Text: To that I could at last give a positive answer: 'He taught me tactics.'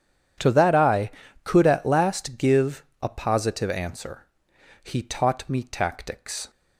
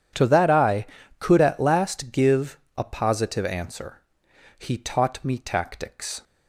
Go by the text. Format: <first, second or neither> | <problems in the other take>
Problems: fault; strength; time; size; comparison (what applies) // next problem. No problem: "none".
neither | starts louder than the rest; strong; the same in both // pauses between "give" and "a"; slight; the same in both